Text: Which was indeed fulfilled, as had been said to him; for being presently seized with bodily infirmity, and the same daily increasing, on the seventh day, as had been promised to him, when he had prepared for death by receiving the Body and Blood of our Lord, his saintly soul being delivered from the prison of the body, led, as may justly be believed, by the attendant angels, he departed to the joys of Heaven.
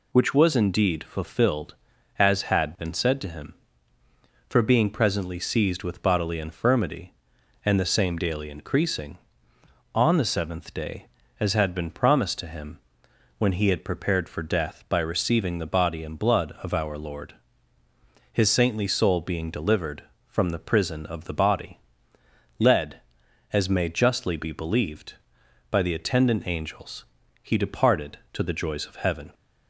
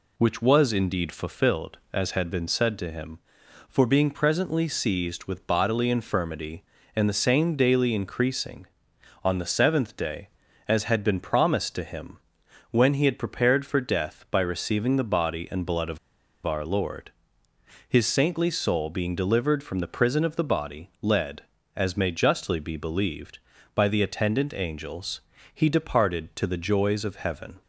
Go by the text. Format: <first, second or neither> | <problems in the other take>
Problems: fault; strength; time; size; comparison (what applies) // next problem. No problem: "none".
first | pauses between "of" and "our"; noticeable; at 15.9 s; 0.47 s long